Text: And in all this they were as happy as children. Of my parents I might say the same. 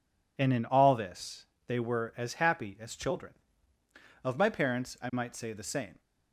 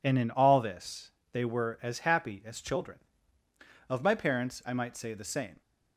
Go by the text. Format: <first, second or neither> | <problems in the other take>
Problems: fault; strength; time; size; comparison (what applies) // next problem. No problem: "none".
neither | pauses between "this" and "they"; slight; the same in both